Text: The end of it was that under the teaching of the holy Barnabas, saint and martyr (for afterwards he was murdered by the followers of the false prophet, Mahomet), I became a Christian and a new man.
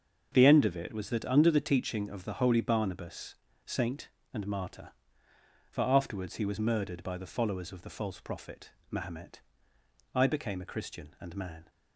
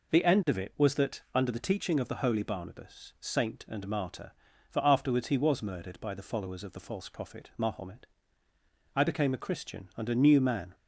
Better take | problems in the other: second | starts louder than the rest; until 1.3 s; 6.5 dB // skips "a new"; at 11.3 s

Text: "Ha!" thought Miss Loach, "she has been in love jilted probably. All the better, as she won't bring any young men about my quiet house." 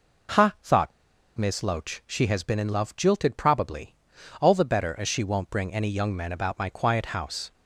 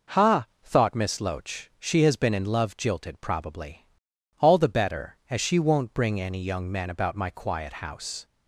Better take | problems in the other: second | pauses between "thought" and "Miss"; noticeable; at 0.9 s; 0.48 s long

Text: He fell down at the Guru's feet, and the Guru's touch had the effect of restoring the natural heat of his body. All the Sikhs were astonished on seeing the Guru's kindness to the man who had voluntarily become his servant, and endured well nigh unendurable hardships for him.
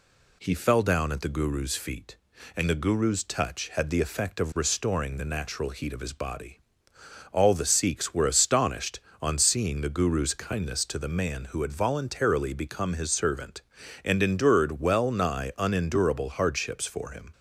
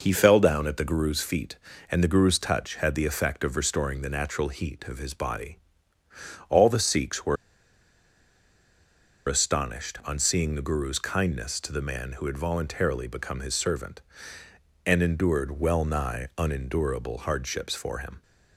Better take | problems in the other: first | pauses between "were" and "astonished"; strong; at 7.3 s; 1.9 s long

